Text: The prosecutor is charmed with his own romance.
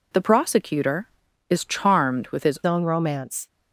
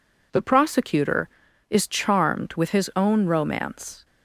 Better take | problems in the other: second | changes voice at "own"; from 2.6 s on; 0.8 s long

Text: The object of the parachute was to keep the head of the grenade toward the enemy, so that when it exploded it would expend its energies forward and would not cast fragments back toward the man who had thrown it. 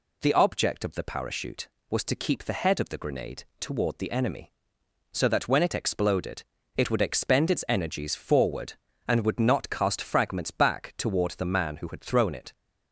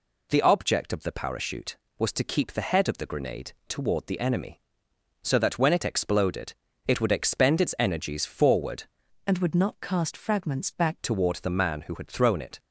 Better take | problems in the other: first | pauses between "grenade" and "toward"; slight; at 3.5 s; 0.16 s long; slight in the first // pauses between "exploded" and "it"; slight; at 6.5 s; 0.34 s long; slight in the first // changes voice from "and" to "back"; from 9.2 to 10.9 s; 1.7 s long

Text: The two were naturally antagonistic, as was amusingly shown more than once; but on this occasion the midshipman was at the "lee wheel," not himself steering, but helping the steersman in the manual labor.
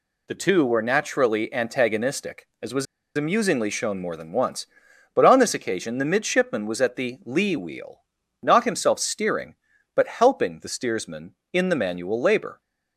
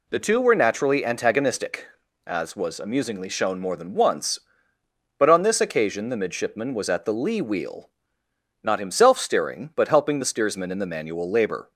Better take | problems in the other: second | pauses between "was" and "amusingly"; slight; at 2.8 s; 0.31 s long

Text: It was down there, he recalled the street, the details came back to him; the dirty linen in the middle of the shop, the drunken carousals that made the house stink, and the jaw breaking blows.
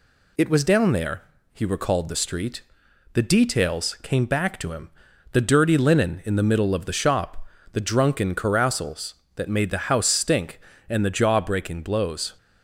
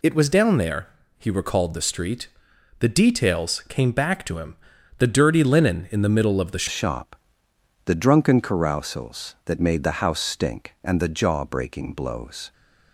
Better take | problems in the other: first | changes voice at "shop"; from 6.6 s on; 5.9 s long

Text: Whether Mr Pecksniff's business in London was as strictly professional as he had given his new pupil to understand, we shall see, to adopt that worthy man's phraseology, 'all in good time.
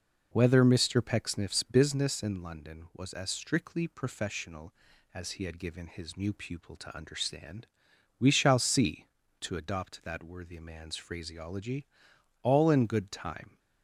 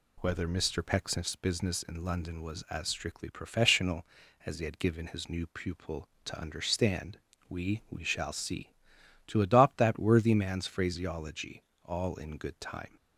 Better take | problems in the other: first | says "we" twice; at 7.8 s

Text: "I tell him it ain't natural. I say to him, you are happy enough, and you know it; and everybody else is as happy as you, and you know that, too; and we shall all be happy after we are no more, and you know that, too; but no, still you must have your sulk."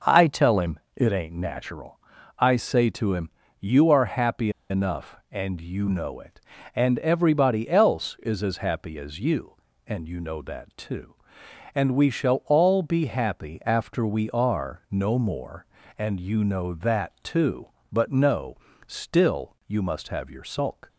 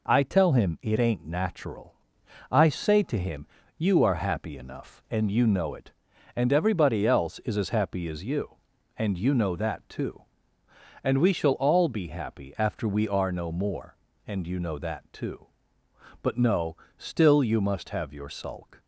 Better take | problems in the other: second | pauses between "him" and "it"; slight; at 0.8 s; 0.16 s long // pauses between "happy" and "enough"; slight; at 4.5 s; 0.19 s long

